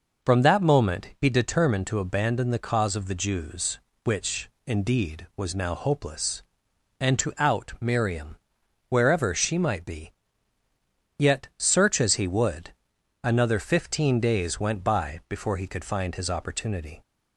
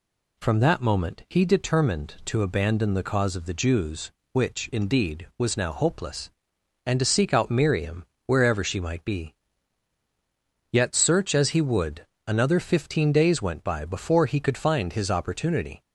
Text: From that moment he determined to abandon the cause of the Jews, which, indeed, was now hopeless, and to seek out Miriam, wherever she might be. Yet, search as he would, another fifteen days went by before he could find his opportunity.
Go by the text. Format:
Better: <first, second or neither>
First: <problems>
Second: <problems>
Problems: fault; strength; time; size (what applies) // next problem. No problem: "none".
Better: second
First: skips "seek"; at 7.3 s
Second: none